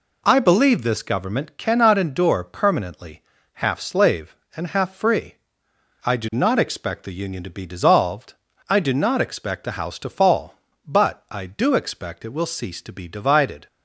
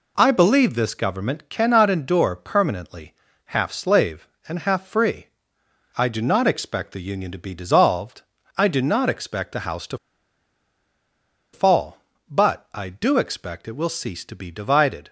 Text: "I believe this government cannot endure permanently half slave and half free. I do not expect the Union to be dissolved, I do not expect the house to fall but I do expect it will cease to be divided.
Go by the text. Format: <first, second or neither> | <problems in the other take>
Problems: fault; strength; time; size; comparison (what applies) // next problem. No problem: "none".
first | pauses between "permanently" and "half"; slight; at 3.1 s; 0.32 s long; slight in the first // pauses between "to" and "fall"; strong; at 9.9 s; 1.5 s long